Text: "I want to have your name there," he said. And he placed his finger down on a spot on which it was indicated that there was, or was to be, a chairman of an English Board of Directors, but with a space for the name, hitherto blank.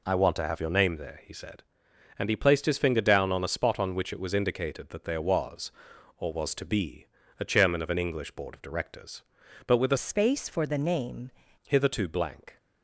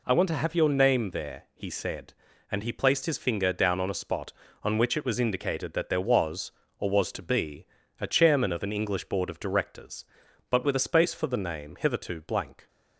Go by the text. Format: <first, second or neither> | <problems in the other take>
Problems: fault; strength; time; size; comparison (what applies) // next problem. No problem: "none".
second | changes voice from "space" to "name"; from 9.9 to 11.3 s; 1.4 s long